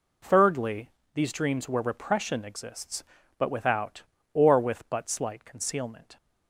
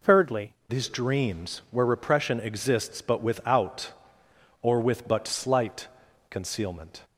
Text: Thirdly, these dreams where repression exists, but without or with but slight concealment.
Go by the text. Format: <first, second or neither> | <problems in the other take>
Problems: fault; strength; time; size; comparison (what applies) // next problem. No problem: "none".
first | changes voice at "these"; from 0.6 s on; 6.4 s long // pauses between "slight" and "concealment"; at 5.8 s; 0.44 s long